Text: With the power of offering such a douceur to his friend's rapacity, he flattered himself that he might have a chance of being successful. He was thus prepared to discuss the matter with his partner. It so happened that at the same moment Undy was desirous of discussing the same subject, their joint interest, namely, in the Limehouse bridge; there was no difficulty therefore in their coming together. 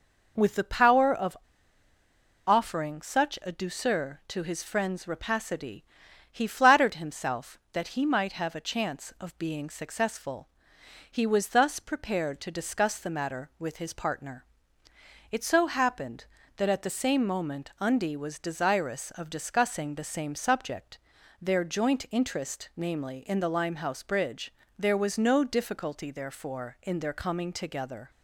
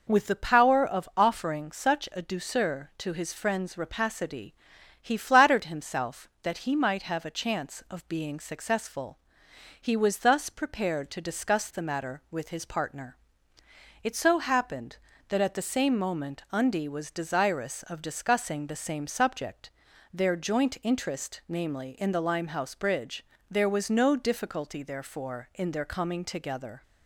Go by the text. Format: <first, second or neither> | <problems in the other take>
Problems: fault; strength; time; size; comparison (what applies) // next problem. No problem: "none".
second | pauses between "of" and "offering"; at 1.3 s; 1.1 s long